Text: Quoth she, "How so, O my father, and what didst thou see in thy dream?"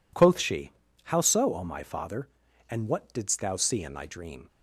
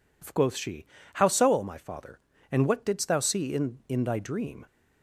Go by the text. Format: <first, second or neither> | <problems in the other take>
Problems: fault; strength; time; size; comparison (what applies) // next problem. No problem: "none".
first | says "in" twice; at 3.8 s